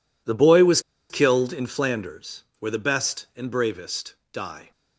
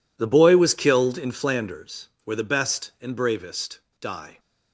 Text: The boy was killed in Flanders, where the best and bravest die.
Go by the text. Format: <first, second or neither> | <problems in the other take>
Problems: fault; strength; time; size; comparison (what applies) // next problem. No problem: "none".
second | pauses between "was" and "killed"; slight; at 0.7 s; 0.30 s long // pauses between "bravest" and "die"; slight; at 4.1 s; 0.18 s long; slight in the second